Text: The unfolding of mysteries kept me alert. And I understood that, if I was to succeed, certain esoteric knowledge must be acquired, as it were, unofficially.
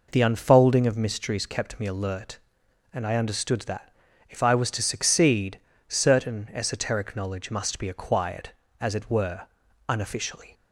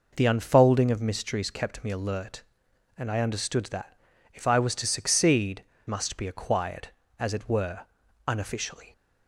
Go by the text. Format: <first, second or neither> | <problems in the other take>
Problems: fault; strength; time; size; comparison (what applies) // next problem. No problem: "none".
first | skips "certain esoteric knowledge"; at 5.7 s